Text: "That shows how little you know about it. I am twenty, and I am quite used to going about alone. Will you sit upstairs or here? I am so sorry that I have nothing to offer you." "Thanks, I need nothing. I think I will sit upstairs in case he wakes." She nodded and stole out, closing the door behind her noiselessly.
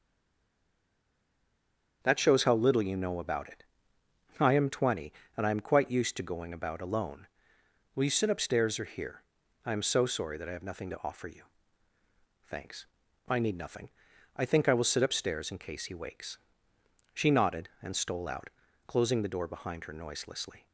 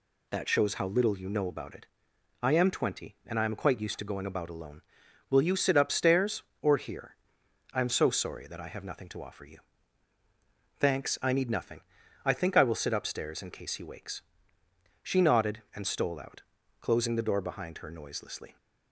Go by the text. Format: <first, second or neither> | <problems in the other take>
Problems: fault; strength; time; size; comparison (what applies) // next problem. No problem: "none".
second | stays silent before the first word; noticeable; until 2.0 s; 2.0 s long // starts louder than the rest; strong; until 3.0 s; 7 dB